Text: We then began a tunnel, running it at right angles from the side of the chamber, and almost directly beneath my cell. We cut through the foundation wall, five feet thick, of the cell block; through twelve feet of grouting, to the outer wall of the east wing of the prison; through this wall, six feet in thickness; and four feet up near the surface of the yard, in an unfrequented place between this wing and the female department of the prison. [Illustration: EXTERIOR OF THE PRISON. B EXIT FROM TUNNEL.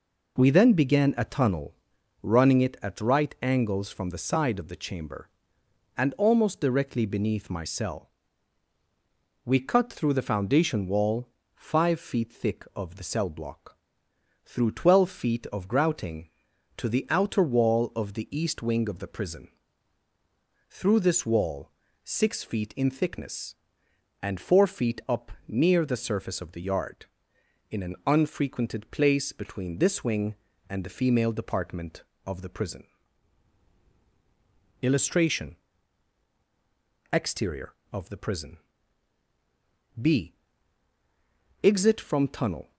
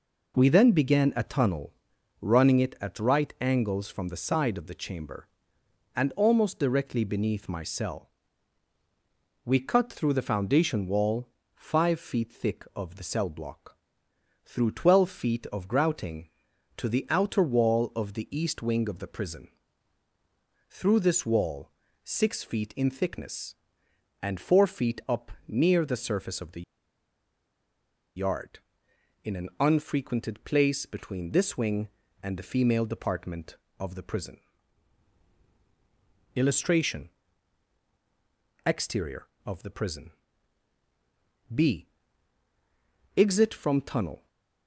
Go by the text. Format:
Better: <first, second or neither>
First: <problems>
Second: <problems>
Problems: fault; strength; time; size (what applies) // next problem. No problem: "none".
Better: first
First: pauses between "up" and "near"; slight; at 25.3 s; 0.16 s long // pauses between "B" and "EXIT"; strong; at 40.3 s; 1.2 s long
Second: pauses between "up" and "near"; slight; at 25.3 s; 0.16 s long // pauses between "the" and "yard"; strong; at 26.6 s; 1.5 s long // pauses between "B" and "EXIT"; strong; at 41.8 s; 1.2 s long